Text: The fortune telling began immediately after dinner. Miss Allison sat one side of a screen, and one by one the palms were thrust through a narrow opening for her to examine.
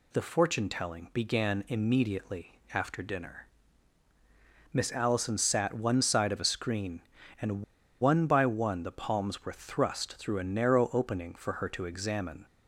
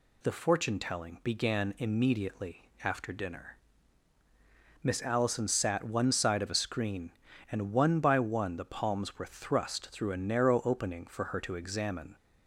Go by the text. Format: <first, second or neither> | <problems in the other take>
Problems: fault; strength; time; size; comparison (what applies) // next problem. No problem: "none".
second | pauses between "and" and "one"; at 7.6 s; 0.38 s long